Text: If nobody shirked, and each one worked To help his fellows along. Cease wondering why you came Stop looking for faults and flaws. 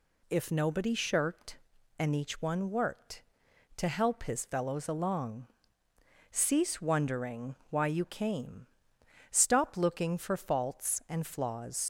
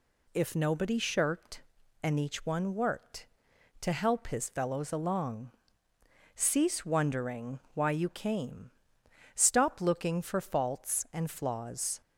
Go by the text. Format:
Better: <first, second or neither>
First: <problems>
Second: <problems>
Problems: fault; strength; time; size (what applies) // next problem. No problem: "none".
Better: second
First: pauses between "wondering" and "why"; slight; at 7.5 s; 0.16 s long // pauses between "came" and "Stop"; noticeable; at 8.6 s; 0.64 s long // leaves "flaws" unfinished; at 11.8 s; 80 ms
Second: pauses between "wondering" and "why"; slight; at 7.5 s; 0.16 s long // pauses between "came" and "Stop"; noticeable; at 8.7 s; 0.64 s long